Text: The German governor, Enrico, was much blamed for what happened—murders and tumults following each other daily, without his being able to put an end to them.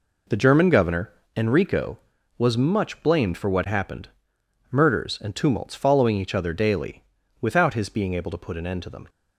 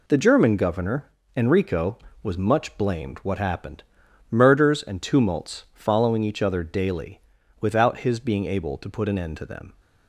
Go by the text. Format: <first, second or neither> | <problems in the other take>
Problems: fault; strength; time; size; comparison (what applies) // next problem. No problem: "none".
first | skips "for"; at 3.1 s